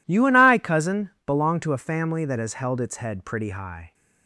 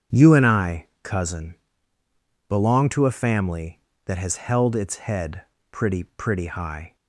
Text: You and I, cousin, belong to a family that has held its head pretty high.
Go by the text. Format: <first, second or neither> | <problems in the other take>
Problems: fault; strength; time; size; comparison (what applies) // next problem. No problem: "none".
first | starts louder than the rest; strong; until 1.3 s; 8 dB // pauses between "head" and "pretty"; slight; at 5.4 s; 0.28 s long // says "pretty" twice; at 6.0 s